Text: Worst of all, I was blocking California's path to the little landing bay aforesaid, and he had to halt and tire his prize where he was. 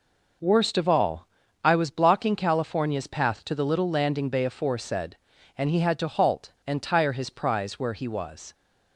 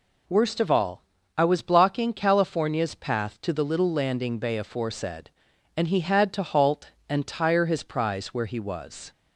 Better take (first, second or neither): neither